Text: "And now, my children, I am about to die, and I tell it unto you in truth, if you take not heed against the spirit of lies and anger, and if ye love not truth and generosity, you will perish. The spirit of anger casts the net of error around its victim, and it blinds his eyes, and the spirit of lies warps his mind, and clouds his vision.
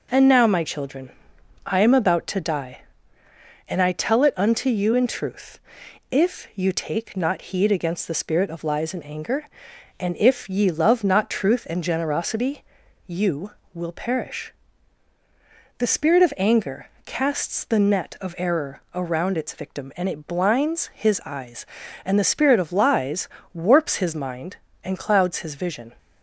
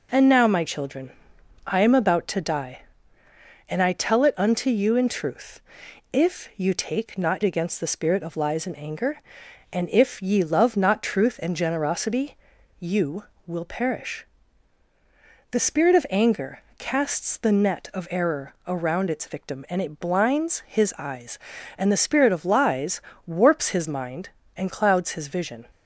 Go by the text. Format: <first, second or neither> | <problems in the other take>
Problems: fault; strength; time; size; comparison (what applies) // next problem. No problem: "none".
first | skips "heed"; at 7.4 s // pauses between "anger" and "casts"; slight; at 16.6 s; 0.16 s long; slight in the first // pauses between "lies" and "warps"; slight; at 23.0 s; 0.24 s long; slight in the first